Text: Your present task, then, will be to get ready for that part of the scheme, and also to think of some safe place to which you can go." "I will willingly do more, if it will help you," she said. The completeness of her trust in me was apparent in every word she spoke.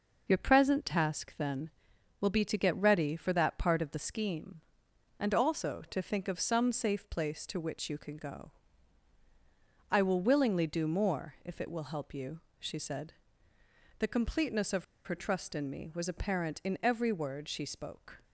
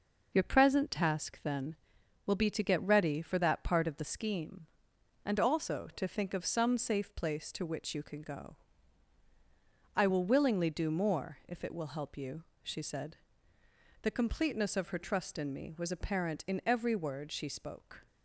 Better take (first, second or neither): second